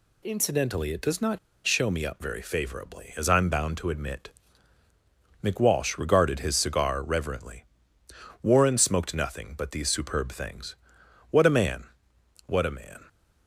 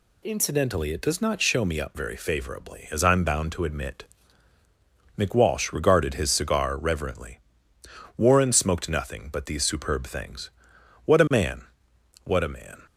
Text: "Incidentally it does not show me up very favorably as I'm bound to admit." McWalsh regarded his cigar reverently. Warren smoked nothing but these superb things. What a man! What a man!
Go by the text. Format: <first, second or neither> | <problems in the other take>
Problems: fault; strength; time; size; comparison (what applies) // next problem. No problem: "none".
second | pauses between "not" and "show"; slight; at 1.3 s; 0.28 s long